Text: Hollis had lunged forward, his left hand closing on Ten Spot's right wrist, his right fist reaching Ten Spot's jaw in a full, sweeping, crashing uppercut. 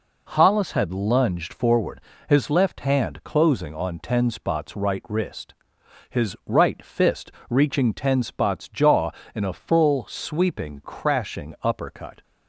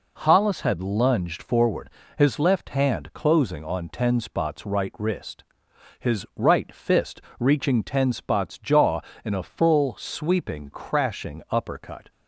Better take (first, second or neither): neither